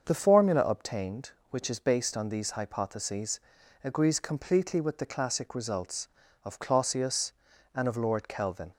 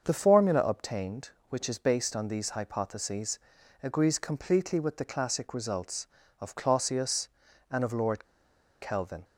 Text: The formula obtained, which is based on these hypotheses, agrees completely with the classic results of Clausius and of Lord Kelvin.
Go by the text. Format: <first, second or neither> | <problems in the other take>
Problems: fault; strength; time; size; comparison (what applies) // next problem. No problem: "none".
first | starts louder than the rest; until 1.0 s; 6.5 dB; also in the first // pauses between "Lord" and "Kelvin"; noticeable; at 8.2 s; 0.56 s long